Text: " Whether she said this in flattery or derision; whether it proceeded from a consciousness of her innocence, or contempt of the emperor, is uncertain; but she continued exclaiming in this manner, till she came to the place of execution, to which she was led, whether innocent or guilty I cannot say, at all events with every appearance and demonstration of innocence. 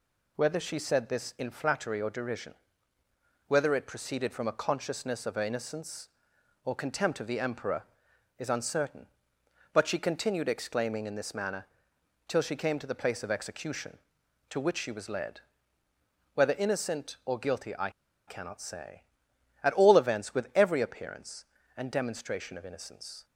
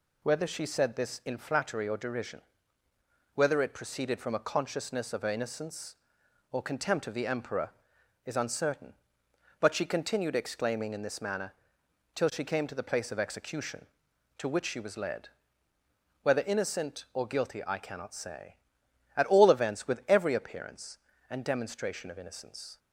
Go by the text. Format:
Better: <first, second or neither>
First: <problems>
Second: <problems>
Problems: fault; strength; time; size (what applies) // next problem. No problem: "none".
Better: second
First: pauses between "I" and "cannot"; at 17.9 s; 0.37 s long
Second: none